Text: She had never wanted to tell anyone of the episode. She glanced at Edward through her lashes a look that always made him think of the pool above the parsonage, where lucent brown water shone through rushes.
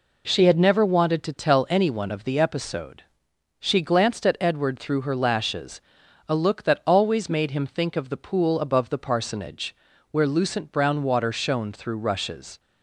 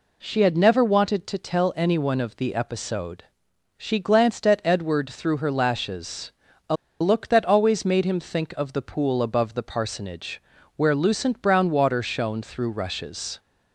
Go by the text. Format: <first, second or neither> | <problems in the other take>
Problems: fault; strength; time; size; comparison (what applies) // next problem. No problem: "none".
first | pauses between "lashes" and "a"; at 6.3 s; 0.38 s long; noticeable in the first // pauses between "a" and "look"; slight; at 6.7 s; 0.25 s long